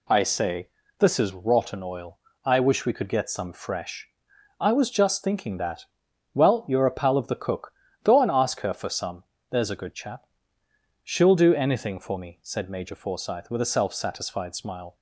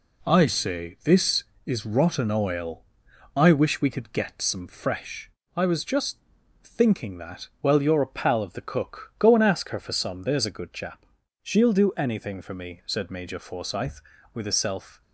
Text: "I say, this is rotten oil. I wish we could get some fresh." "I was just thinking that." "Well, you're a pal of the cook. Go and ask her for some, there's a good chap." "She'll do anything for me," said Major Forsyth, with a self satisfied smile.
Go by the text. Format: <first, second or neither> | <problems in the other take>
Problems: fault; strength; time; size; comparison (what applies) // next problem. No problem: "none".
first | pauses between "just" and "thinking"; noticeable; at 6.1 s; 0.46 s long // stops before "satisfied smile"; at 15.0 s